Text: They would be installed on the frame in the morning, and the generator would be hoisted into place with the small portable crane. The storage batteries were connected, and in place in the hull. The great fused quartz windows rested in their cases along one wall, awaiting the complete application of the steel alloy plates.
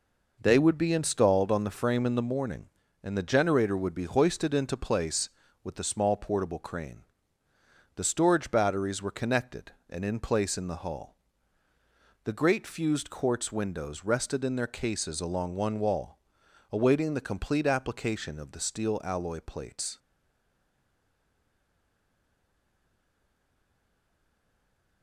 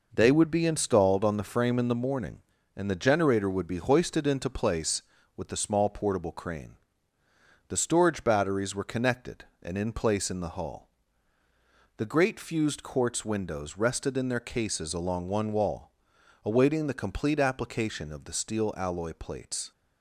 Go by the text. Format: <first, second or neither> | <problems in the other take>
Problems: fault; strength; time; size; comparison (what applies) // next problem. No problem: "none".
second | stays silent after the last word; strong; from 19.9 s on; 5.1 s long